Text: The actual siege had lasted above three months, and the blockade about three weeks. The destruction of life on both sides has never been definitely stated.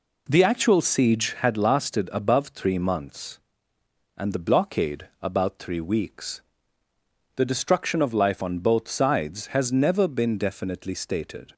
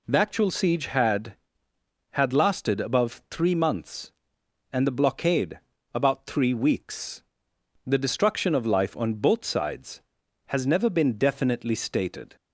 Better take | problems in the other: first | says "had" twice; at 2.1 s // pauses between "blockade" and "about"; slight; at 5.5 s; 0.34 s long

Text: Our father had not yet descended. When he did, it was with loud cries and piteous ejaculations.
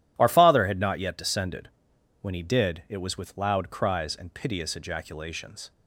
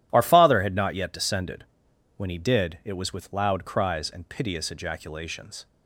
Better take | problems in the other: neither | none

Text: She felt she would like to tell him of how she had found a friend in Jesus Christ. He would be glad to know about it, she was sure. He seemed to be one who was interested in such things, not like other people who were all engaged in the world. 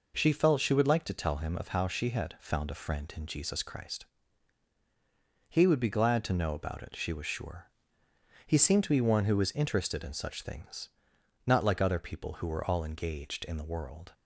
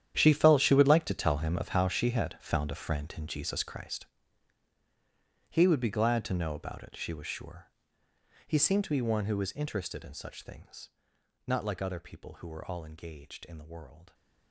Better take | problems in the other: first | gets quieter; strong; throughout; 15.5 dB

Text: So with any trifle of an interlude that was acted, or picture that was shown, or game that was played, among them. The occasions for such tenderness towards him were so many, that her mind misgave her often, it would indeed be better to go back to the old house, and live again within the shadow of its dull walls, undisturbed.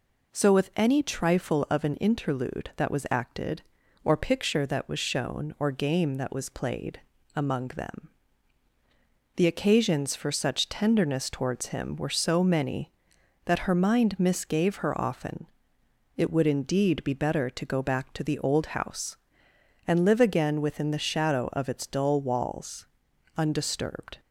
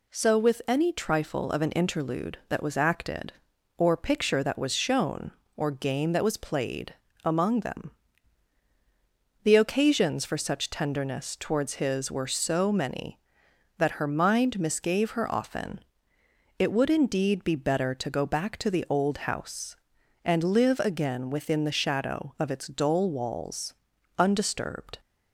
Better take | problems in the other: first | says "his" for "him"; at 11.7 s

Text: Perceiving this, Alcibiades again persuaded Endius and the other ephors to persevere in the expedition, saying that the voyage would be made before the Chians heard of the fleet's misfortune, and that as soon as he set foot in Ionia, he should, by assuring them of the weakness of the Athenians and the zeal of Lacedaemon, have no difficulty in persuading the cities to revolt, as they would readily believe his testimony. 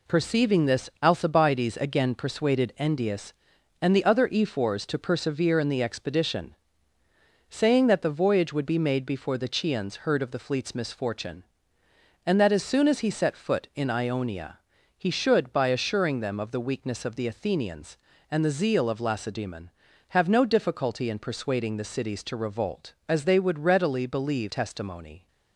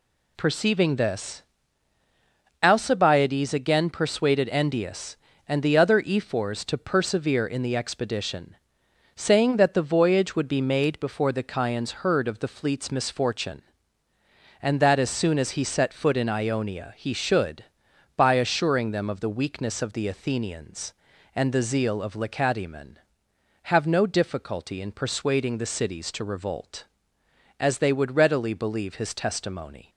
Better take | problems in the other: second | skips "his"; at 24.5 s

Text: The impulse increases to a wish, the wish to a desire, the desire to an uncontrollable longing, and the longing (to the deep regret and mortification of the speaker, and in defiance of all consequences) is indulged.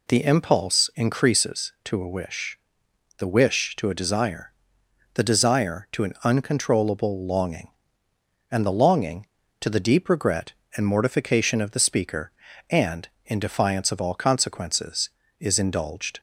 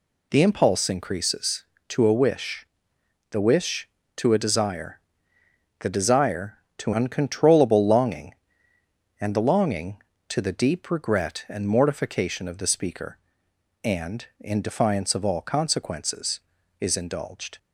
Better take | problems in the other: first | skips "an"; at 6.9 s

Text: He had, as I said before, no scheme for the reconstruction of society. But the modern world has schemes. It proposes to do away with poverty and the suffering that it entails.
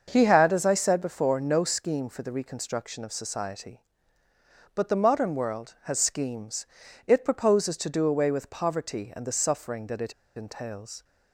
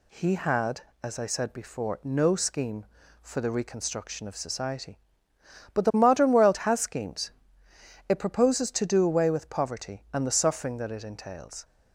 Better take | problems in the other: second | starts louder than the rest; until 1.1 s; 6.5 dB // pauses between "it" and "entails"; slight; at 10.1 s; 0.25 s long

